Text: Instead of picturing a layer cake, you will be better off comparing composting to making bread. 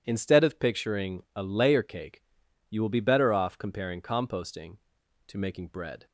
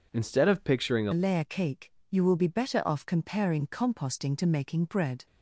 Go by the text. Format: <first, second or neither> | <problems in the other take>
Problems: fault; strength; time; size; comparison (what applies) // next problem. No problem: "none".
first | changes voice at "layer"; from 1.1 s on; 4.1 s long